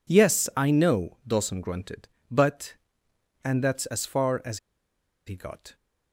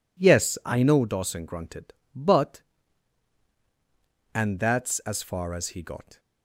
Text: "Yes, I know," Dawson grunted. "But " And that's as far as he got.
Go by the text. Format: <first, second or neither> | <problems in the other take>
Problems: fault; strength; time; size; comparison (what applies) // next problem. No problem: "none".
second | pauses between "as" and "he"; noticeable; at 4.5 s; 0.67 s long